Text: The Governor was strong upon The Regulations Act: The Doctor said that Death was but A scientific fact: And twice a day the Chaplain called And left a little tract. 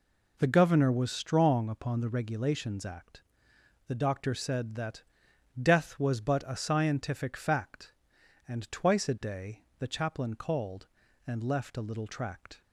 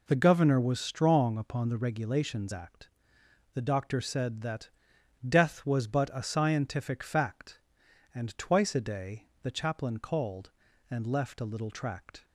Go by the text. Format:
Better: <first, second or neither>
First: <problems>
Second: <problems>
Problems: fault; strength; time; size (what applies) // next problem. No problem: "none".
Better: neither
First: pauses between "that" and "Death"; noticeable; at 5.0 s; 0.58 s long // pauses between "day" and "the"; slight; at 9.6 s; 0.16 s long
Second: pauses between "that" and "Death"; noticeable; at 4.6 s; 0.58 s long // pauses between "day" and "the"; slight; at 9.2 s; 0.16 s long